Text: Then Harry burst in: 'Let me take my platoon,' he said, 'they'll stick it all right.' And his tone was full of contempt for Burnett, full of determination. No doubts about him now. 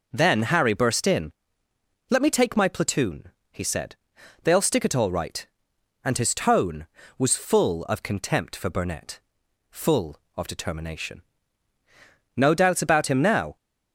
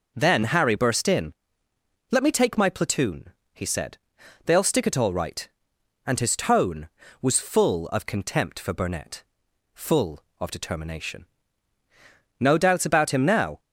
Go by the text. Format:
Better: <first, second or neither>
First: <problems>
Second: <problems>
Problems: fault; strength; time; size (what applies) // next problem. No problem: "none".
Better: neither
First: none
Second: none